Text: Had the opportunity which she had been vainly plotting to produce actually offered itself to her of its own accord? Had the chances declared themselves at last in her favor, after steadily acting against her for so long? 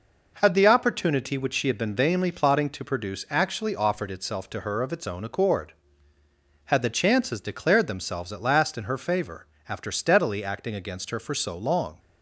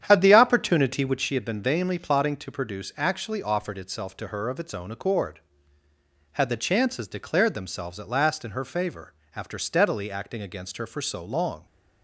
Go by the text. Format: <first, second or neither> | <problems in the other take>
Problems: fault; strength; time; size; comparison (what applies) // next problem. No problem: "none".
first | starts louder than the rest; strong; until 1.3 s; 9.5 dB